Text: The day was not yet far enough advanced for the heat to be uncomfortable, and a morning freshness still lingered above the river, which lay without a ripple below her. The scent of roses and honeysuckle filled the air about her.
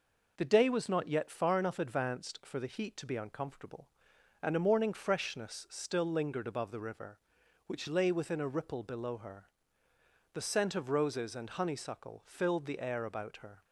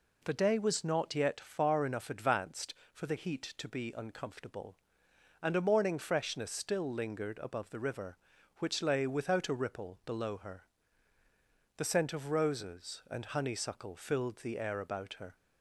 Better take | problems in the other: second | says "within" for "without"; at 8.1 s

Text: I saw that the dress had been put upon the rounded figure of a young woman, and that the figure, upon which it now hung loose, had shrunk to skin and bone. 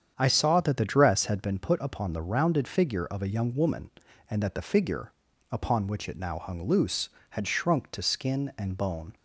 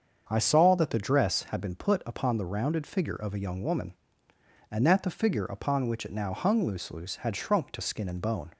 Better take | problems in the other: first | starts louder than the rest; until 1.3 s; 7 dB; strong in the first // says "loose" twice; at 6.9 s

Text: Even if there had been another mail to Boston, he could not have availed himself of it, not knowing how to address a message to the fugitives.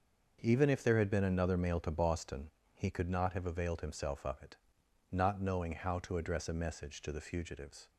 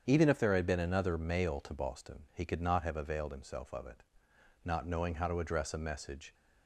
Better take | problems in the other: first | starts louder than the rest; strong; until 1.0 s; 7.5 dB; also in the first // stops before "to the fugitives"; at 6.3 s

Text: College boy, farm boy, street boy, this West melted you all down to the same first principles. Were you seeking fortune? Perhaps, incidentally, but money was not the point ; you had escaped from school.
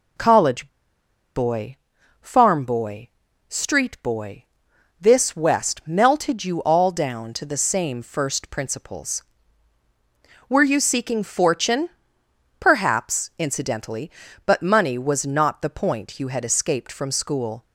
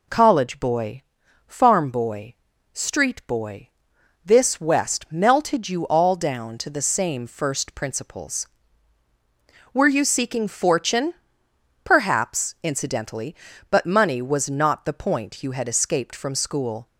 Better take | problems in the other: second | pauses between "College" and "boy"; noticeable; at 0.6 s; 0.68 s long

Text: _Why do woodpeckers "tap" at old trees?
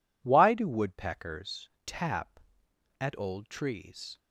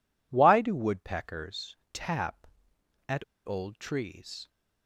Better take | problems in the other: first | pauses between "woodpeckers" and "tap"; slight; at 1.7 s; 0.16 s long; slight in the first // pauses between "at" and "old"; slight; at 3.2 s; 0.21 s long

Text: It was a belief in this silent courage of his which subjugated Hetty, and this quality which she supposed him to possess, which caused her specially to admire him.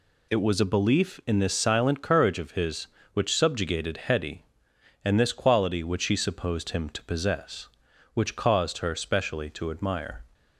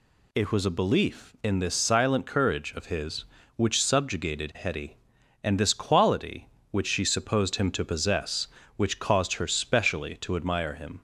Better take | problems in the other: second | stops before "him"; at 10.3 s

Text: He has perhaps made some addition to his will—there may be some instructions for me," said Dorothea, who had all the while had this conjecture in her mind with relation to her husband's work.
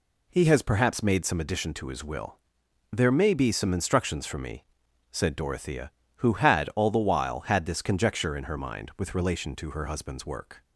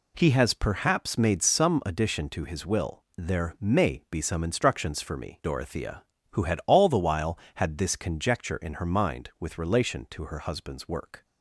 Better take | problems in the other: first | skips "said"; at 5.4 s

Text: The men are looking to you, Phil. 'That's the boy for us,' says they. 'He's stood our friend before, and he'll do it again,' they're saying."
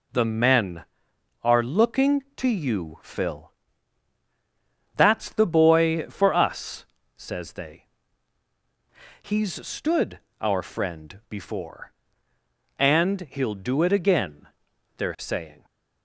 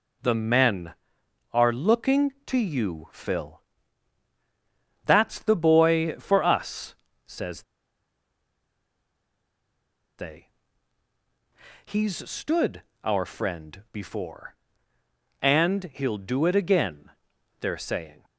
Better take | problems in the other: first | pauses between "says" and "they"; strong; at 7.6 s; 2.5 s long // pauses between "stood" and "our"; slight; at 12.8 s; 0.22 s long; slight in the first

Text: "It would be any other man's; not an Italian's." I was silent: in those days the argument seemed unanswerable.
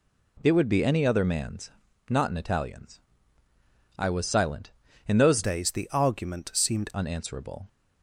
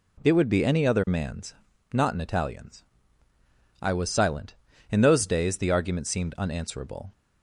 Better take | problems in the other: second | changes voice from "days" to "seemed"; from 5.4 to 6.9 s; 1.5 s long

